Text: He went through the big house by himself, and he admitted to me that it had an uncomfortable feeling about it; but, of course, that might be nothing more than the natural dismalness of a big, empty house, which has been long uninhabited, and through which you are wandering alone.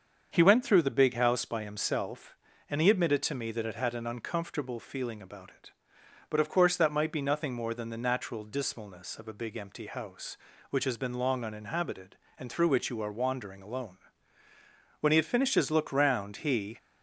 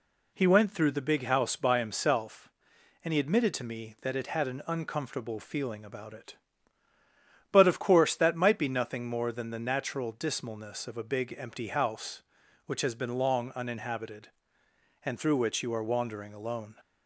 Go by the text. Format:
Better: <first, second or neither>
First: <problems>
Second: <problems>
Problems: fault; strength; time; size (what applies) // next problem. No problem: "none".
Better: second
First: starts louder than the rest; until 1.3 s; 7 dB // goes on to say "When he had finished his look round he"; strong; from 15.0 s on; 1.7 s long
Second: none